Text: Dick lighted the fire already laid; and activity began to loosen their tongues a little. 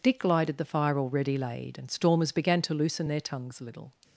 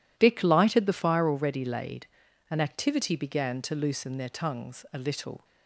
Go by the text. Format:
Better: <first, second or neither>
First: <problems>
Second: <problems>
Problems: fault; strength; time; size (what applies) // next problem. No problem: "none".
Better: second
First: says "stormers" for "activity"; at 1.8 s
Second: none